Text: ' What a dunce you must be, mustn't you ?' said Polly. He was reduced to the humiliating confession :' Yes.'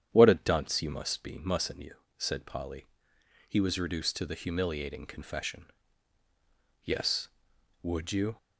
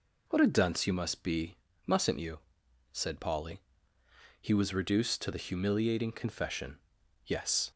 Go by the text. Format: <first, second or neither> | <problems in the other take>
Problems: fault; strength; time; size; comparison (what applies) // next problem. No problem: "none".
second | starts louder than the rest; strong; until 1.1 s; 10 dB // goes on to say "Would you"; from 7.8 s on; 0.54 s long